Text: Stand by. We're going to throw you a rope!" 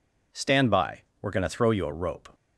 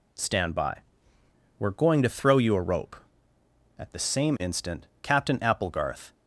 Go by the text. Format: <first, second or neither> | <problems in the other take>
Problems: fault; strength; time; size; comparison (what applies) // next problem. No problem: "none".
first | goes on to say "At the same instant Captain Applegarth"; strong; from 3.7 s on; 2.3 s long